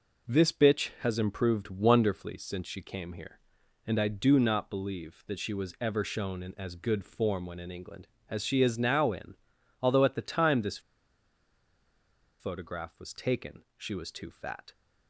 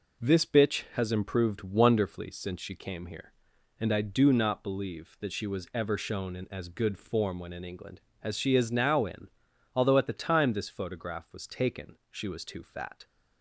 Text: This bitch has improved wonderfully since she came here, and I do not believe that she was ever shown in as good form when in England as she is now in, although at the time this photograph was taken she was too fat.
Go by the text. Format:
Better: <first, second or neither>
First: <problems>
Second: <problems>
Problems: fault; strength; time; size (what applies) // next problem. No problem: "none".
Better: second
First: pauses between "this" and "photograph"; strong; at 10.7 s; 1.6 s long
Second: none